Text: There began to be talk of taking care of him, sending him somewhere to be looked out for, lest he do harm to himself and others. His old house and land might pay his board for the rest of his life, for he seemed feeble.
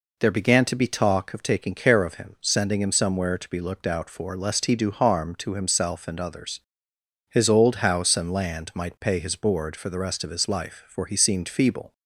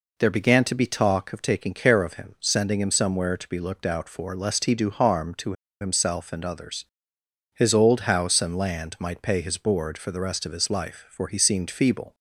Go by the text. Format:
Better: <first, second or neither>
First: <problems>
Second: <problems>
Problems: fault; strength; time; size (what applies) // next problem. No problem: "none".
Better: first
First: none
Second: pauses between "to" and "himself"; slight; at 5.5 s; 0.28 s long